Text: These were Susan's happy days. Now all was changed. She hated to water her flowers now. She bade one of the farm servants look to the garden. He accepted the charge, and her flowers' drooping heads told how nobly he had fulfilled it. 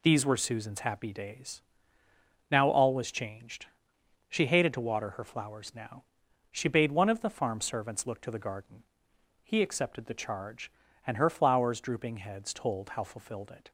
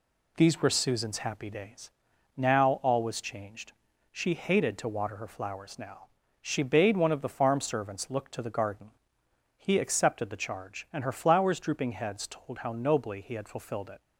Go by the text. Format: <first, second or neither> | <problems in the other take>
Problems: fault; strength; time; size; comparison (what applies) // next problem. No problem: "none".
second | skips "nobly he had"; at 13.0 s